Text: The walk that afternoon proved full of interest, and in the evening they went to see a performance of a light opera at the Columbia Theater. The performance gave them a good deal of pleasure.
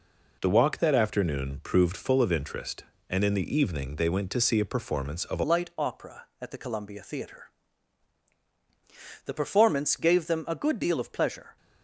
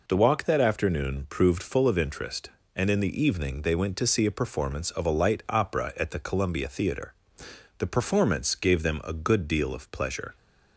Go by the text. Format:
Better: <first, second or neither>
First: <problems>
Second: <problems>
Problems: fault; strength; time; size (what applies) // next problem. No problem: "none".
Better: second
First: changes voice at "light"; from 5.4 s on; 6.1 s long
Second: none